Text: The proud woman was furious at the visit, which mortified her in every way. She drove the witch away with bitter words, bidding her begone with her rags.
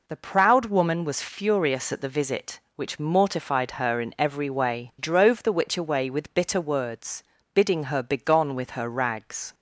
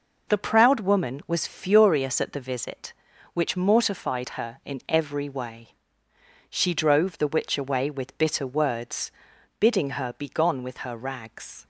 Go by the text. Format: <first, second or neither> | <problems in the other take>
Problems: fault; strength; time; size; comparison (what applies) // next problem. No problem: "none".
second | skips "She"; at 4.9 s